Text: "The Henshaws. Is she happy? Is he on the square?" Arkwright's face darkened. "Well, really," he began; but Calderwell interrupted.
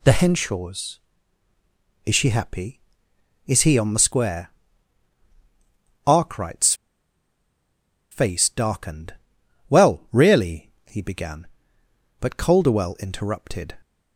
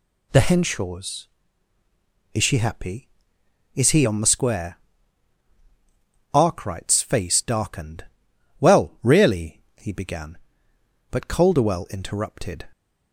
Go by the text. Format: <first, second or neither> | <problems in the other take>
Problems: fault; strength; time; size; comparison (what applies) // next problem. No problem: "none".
second | pauses between "Arkwright's" and "face"; strong; at 6.7 s; 1.3 s long